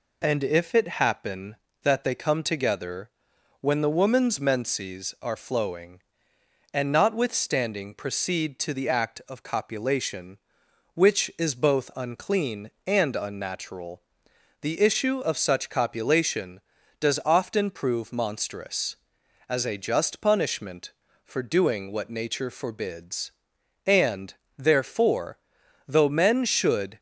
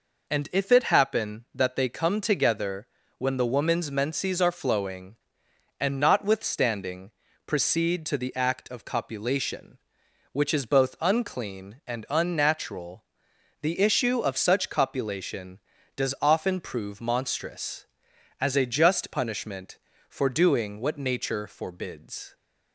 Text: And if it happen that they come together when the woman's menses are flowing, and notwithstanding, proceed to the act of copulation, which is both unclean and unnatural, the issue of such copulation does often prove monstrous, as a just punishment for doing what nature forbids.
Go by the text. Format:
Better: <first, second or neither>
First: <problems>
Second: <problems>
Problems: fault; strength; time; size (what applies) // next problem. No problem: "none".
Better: second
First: pauses between "together" and "when"; noticeable; at 3.1 s; 0.48 s long // goes on to say "And therefore though men should"; strong; from 23.8 s on; 3.1 s long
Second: pauses between "together" and "when"; slight; at 2.8 s; 0.30 s long